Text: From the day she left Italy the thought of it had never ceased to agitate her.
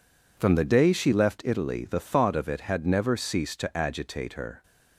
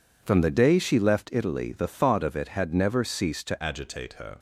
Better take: first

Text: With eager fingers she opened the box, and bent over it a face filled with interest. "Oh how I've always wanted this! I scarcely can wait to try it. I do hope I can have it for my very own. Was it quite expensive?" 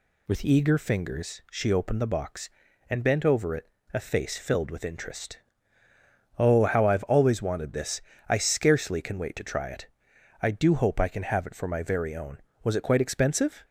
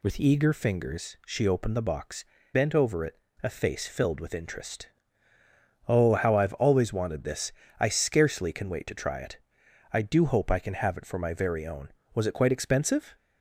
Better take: first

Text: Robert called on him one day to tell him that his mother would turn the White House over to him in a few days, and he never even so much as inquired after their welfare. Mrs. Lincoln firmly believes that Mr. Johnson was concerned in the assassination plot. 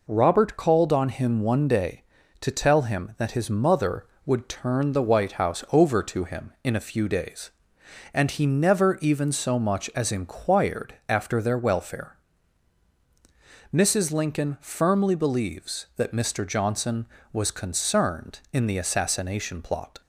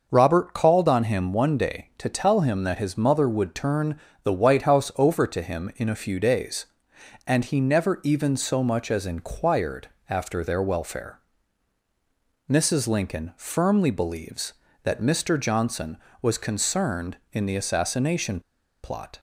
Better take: first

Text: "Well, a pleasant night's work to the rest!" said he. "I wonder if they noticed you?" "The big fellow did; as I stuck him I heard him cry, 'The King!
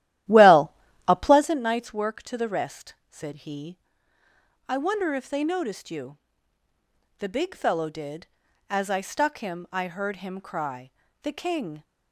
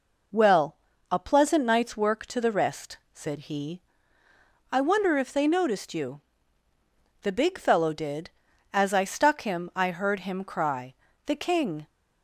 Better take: second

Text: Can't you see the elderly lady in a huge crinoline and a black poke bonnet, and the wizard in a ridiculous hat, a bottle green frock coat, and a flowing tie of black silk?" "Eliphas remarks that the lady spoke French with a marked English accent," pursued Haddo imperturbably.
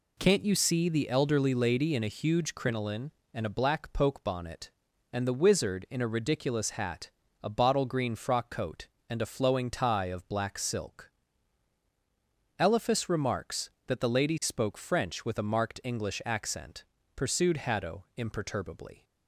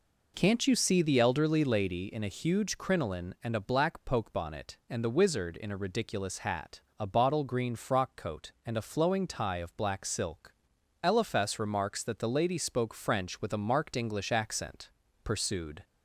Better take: first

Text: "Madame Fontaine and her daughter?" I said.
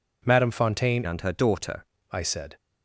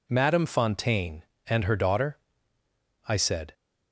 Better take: second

